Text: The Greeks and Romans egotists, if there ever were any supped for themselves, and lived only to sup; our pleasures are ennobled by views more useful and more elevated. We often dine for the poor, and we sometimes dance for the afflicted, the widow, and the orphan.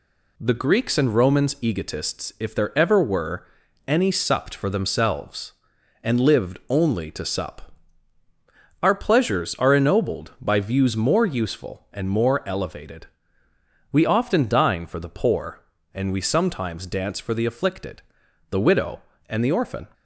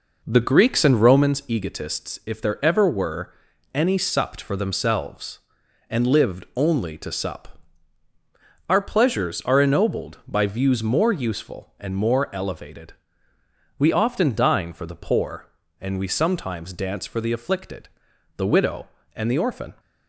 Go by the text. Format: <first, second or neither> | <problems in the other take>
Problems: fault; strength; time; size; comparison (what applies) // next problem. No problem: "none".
first | starts louder than the rest; noticeable; until 1.3 s; 5 dB // pauses between "were" and "any"; at 3.3 s; 0.42 s long; also in the first